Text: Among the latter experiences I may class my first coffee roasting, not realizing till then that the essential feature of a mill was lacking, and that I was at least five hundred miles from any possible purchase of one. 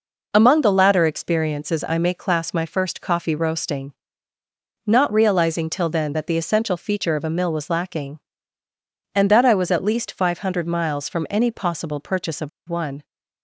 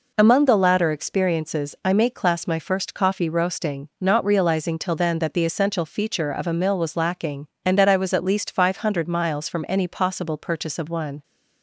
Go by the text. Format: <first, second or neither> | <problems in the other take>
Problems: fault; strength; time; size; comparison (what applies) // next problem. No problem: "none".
second | pauses between "of" and "one"; slight; at 12.4 s; 0.19 s long